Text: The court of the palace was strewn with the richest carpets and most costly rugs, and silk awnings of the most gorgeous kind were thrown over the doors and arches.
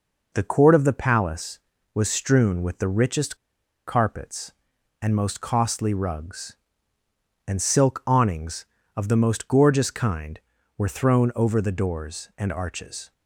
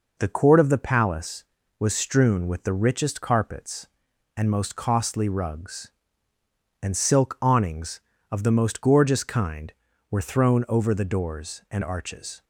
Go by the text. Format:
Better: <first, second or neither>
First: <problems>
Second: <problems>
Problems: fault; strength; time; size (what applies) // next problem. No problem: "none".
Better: second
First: pauses between "richest" and "carpets"; noticeable; at 3.3 s; 0.51 s long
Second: none